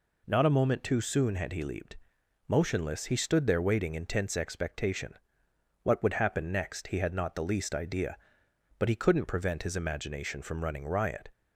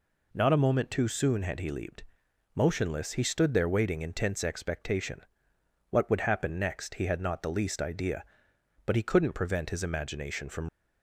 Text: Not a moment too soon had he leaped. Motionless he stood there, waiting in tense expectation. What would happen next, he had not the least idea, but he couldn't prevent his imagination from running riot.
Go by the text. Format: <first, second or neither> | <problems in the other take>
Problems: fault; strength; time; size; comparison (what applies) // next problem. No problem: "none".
first | stops before "running riot"; at 10.6 s